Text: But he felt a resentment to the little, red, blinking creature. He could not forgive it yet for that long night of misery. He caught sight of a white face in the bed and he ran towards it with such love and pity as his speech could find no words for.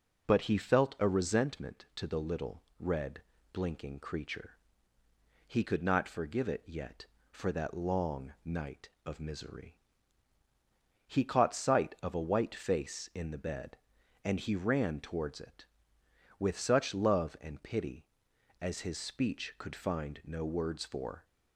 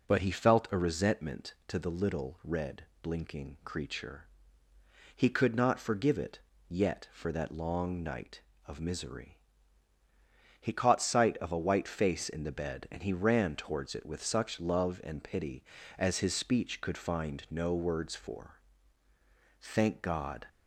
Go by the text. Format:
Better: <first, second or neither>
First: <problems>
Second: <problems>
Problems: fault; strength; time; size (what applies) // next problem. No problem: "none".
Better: first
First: none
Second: pauses between "it" and "yet"; slight; at 6.3 s; 0.30 s long // goes on to say "Thank God"; noticeable; from 19.6 s on; 0.84 s long